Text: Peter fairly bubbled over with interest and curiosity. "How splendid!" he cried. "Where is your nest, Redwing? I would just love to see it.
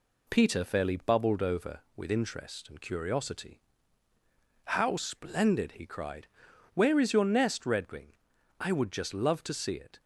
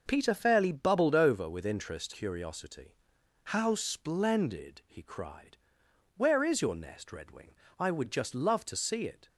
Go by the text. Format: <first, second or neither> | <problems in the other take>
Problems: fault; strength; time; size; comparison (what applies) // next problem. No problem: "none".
first | skips "and"; at 2.1 s